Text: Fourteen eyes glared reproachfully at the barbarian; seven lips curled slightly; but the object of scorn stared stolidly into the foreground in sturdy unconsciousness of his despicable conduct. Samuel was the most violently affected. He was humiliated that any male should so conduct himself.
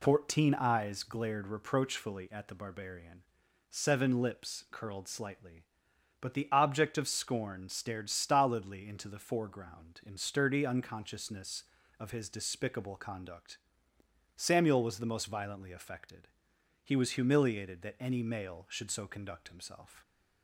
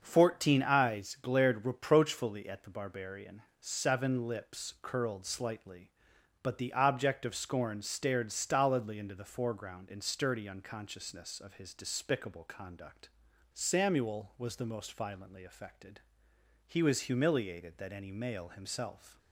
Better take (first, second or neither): first